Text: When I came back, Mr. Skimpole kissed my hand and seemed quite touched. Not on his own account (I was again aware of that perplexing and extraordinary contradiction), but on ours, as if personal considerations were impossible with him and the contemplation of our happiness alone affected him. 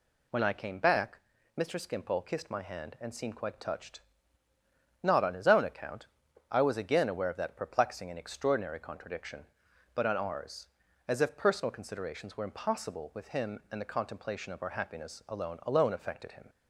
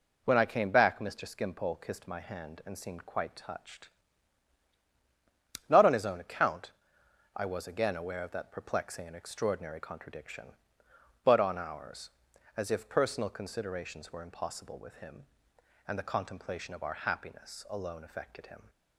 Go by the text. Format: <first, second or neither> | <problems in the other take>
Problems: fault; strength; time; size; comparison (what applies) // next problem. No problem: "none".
second | says "alone" twice; at 15.6 s